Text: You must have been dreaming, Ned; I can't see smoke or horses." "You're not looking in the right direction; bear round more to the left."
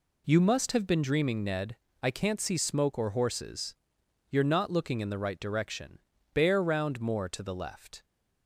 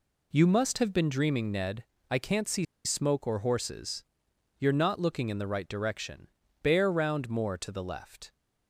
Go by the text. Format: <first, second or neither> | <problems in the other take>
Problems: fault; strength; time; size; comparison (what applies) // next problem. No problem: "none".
first | pauses between "see" and "smoke"; slight; at 2.6 s; 0.20 s long